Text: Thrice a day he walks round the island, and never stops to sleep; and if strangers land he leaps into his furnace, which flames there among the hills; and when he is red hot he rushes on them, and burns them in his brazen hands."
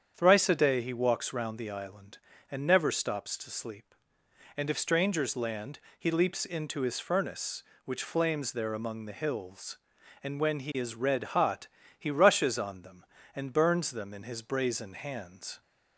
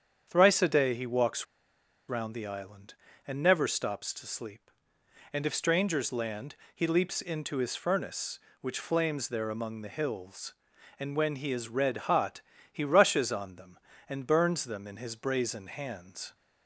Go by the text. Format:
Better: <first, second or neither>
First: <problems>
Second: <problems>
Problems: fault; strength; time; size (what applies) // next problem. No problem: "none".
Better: first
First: starts louder than the rest; strong; until 1.1 s; 8 dB // pauses between "land" and "he"; slight; at 5.7 s; 0.22 s long // pauses between "hot" and "he"; slight; at 11.6 s; 0.32 s long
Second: starts louder than the rest; strong; until 1.3 s; 8 dB // pauses between "walks" and "round"; noticeable; at 1.4 s; 0.63 s long // pauses between "land" and "he"; slight; at 6.5 s; 0.22 s long // pauses between "hot" and "he"; slight; at 12.4 s; 0.32 s long